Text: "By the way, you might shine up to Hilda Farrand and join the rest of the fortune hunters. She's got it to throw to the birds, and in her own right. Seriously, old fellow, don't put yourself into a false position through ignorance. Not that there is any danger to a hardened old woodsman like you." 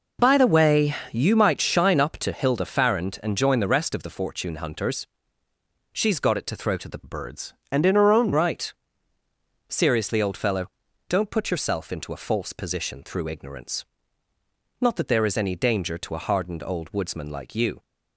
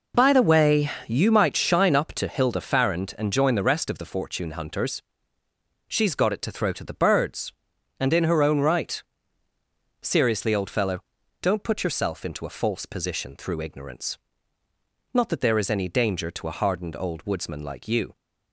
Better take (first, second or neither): second